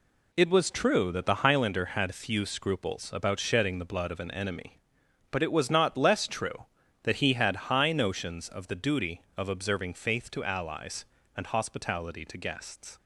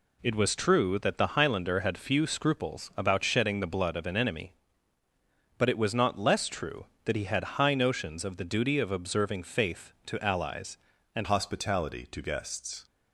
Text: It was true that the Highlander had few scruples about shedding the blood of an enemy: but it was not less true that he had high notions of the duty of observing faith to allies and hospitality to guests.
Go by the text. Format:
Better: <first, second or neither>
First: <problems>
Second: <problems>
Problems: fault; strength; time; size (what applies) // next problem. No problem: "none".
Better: first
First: none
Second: changes voice at "hospitality"; from 11.2 s on; 1.6 s long